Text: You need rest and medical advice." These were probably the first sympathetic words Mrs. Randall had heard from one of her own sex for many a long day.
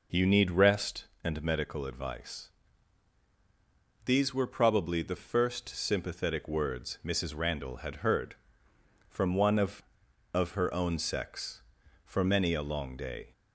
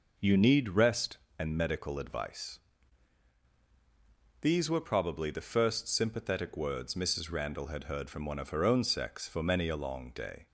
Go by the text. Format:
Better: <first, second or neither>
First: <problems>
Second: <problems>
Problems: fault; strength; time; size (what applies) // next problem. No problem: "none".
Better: second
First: says "of" twice; at 10.3 s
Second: none